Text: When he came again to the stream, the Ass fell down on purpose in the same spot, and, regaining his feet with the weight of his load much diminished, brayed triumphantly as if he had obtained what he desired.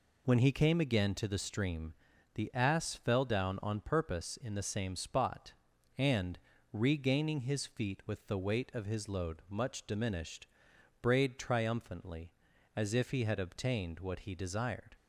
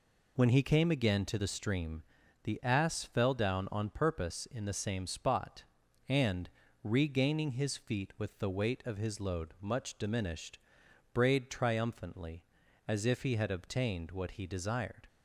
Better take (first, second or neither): neither